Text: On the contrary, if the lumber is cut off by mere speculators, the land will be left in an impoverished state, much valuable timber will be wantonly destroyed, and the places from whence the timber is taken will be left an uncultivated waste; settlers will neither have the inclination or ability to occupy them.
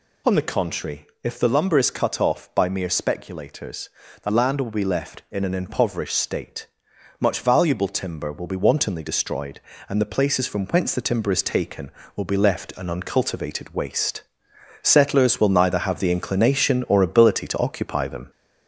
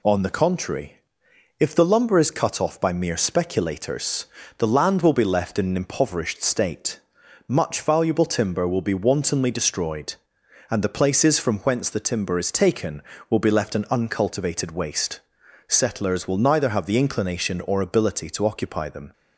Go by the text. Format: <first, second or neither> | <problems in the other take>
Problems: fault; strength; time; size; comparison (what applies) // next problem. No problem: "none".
second | gets louder; slight; throughout; 3.5 dB